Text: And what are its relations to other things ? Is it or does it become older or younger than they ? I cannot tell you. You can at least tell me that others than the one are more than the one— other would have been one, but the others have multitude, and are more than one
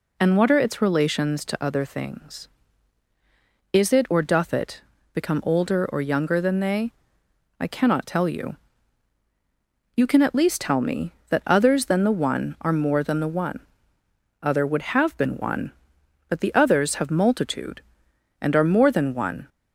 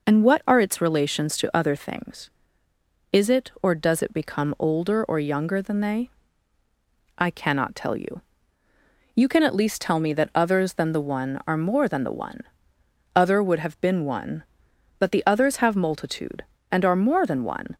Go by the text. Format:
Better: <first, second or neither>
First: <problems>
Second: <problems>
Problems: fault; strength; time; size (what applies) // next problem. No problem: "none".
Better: second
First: says "doth" for "does"; at 4.2 s // pauses between "it" and "become"; slight; at 4.8 s; 0.32 s long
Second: none